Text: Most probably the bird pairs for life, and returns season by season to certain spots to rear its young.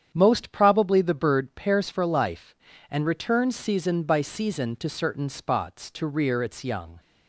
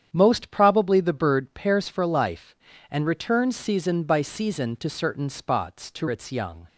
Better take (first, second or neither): first